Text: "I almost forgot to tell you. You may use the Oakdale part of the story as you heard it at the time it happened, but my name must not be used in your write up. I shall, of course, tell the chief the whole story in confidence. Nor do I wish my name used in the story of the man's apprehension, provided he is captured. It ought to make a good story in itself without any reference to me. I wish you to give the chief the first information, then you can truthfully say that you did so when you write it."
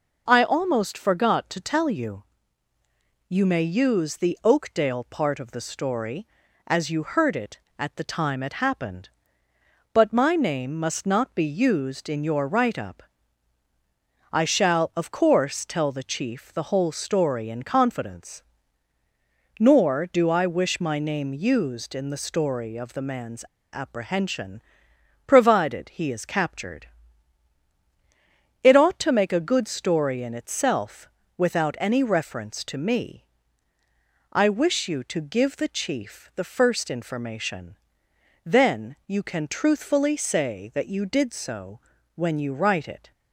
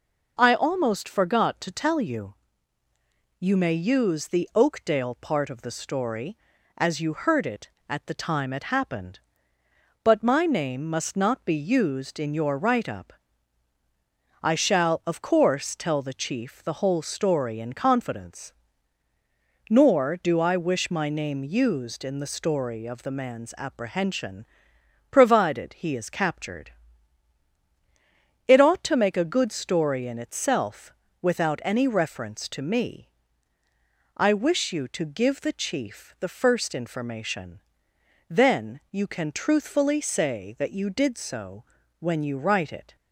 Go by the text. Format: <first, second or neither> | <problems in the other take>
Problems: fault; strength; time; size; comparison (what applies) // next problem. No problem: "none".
second | pauses between "man's" and "apprehension"; slight; at 23.4 s; 0.29 s long // pauses between "itself" and "without"; slight; at 31.0 s; 0.26 s long; slight in the second // pauses between "so" and "when"; slight; at 41.7 s; 0.36 s long; slight in the second